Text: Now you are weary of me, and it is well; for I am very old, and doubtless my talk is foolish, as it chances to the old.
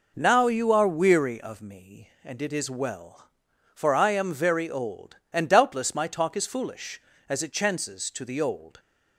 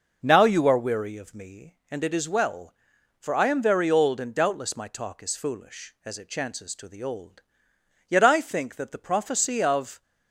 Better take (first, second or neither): first